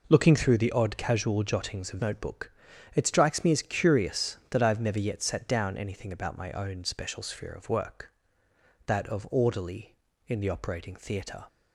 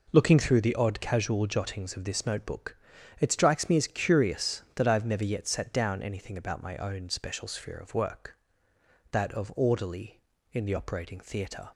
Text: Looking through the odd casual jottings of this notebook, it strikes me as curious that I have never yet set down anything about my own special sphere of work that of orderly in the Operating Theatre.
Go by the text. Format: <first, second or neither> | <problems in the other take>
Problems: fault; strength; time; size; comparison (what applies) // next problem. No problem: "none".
second | skips "this"; at 1.9 s